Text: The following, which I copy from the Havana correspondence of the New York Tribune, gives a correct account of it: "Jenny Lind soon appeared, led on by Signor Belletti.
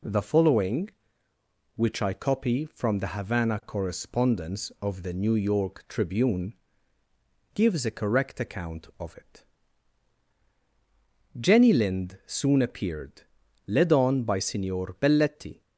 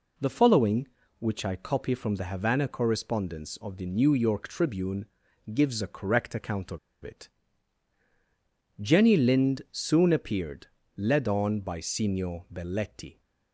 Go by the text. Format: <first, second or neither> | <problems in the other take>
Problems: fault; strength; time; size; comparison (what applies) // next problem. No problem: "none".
first | pauses between "of" and "it"; slight; at 6.7 s; 0.24 s long